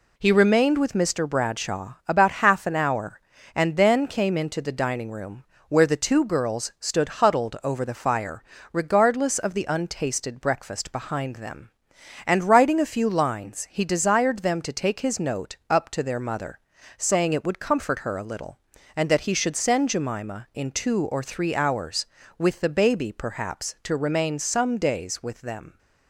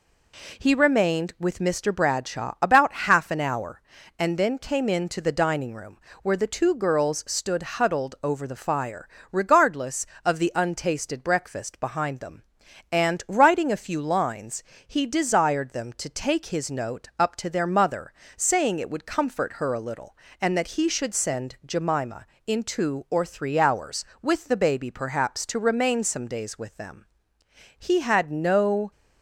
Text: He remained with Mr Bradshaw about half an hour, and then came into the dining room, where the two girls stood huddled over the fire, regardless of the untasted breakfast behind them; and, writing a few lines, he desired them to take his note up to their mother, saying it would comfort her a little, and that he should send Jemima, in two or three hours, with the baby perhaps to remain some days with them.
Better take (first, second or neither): first